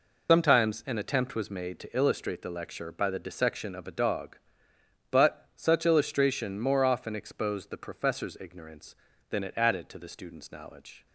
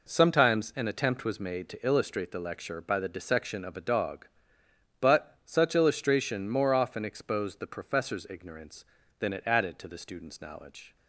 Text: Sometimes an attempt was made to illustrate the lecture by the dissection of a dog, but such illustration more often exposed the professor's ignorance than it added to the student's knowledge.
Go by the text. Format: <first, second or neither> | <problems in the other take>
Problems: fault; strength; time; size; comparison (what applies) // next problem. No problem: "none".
second | loses the start of "Sometimes"; at 0.2 s; 130 ms